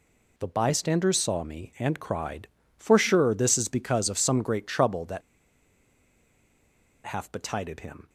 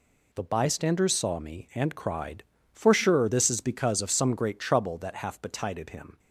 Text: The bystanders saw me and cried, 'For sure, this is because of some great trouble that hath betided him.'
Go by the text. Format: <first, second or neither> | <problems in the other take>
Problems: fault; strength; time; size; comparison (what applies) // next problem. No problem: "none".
second | pauses between "that" and "hath"; strong; at 5.2 s; 1.8 s long